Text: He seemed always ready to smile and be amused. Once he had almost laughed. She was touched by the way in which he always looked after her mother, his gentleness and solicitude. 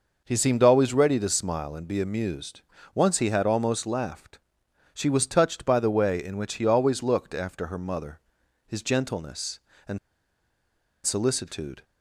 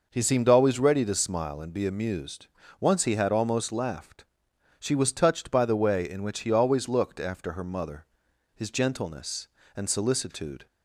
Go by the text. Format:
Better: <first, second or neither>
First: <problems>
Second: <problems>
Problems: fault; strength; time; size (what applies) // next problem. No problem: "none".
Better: second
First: pauses between "and" and "solicitude"; at 9.9 s; 1.0 s long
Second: none